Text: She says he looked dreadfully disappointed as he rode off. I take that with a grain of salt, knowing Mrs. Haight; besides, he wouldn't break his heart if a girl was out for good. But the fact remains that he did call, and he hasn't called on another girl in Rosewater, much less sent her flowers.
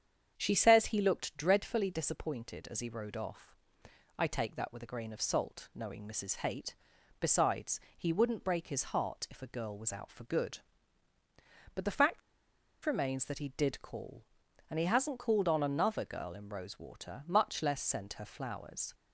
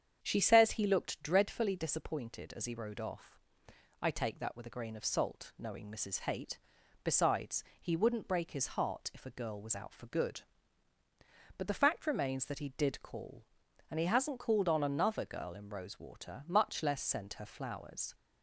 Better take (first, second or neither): second